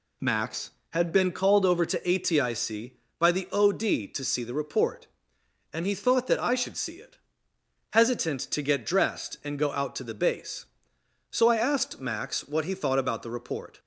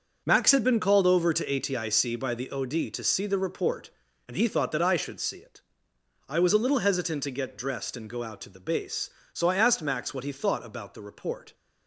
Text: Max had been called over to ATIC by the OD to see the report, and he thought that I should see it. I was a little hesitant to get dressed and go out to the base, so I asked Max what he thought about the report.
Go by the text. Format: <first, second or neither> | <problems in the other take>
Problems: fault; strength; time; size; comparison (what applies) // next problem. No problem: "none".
second | skips "I was a little"; at 7.5 s